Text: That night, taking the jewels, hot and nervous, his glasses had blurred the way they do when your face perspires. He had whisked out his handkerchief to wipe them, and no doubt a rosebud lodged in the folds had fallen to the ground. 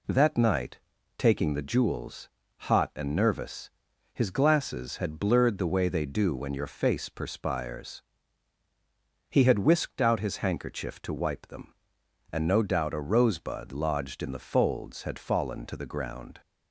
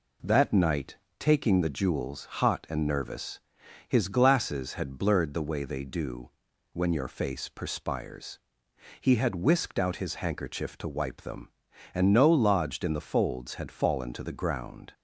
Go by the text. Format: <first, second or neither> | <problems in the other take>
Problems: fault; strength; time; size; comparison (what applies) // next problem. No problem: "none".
first | pauses between "do" and "when"; at 6.2 s; 0.44 s long // skips "doubt a rosebud"; at 12.2 s